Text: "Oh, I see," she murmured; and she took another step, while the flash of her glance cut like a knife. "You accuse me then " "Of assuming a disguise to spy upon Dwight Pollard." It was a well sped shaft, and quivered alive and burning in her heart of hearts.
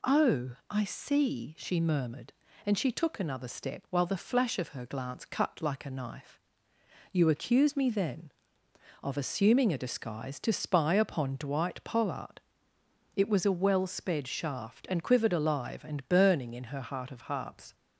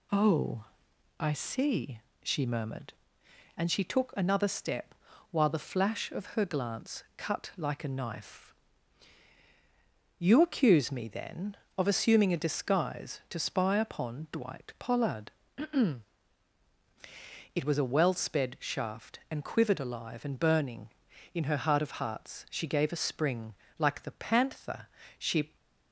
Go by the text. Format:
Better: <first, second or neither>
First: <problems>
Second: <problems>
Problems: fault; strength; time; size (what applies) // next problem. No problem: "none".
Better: first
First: none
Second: goes on to say "She gave a spring like the panther she"; strong; from 22.5 s on; 3.0 s long